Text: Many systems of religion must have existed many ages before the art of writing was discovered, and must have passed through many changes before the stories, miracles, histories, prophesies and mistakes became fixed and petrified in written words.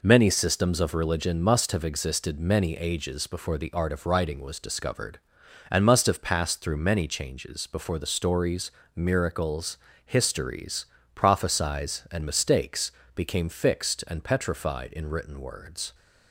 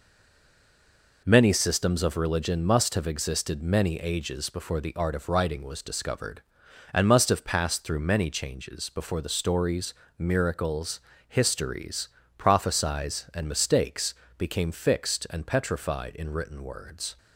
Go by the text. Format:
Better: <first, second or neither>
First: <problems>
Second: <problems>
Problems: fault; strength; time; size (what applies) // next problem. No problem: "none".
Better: first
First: pauses between "mistakes" and "became"; slight; at 12.9 s; 0.24 s long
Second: stays silent before the first word; noticeable; until 1.2 s; 1.2 s long // pauses between "mistakes" and "became"; slight; at 14.1 s; 0.24 s long